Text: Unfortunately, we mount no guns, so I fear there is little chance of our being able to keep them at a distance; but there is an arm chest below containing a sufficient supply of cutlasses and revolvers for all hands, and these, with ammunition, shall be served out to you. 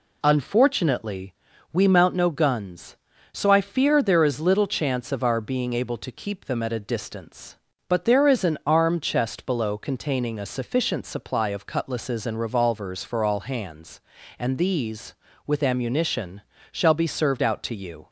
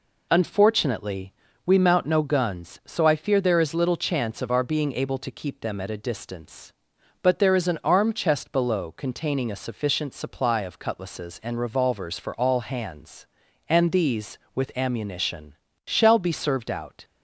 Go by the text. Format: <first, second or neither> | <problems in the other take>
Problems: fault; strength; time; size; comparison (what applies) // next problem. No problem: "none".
first | stops before "to you"; at 17.0 s